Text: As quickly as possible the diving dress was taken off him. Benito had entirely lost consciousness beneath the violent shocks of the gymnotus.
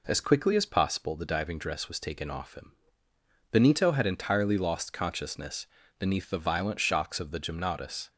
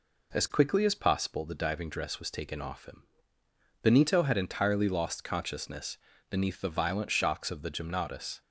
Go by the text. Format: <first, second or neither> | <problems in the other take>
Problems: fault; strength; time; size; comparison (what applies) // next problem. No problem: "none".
neither | pauses between "consciousness" and "beneath"; slight; the same in both